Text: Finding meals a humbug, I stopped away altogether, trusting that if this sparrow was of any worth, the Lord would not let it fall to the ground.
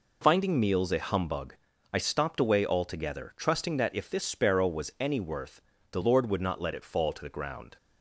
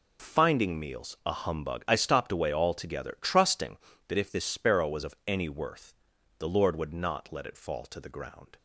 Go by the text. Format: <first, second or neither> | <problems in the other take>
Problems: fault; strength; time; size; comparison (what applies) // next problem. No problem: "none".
second | skips "of"; at 4.9 s